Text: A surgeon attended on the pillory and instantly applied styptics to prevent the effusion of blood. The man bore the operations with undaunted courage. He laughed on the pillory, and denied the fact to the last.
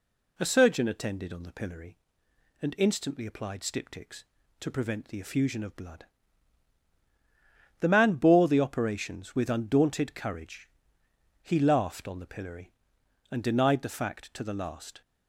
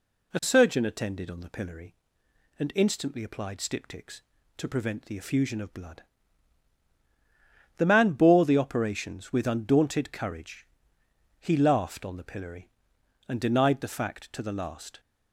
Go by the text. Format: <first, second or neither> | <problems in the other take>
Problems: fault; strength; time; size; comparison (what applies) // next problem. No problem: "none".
neither | none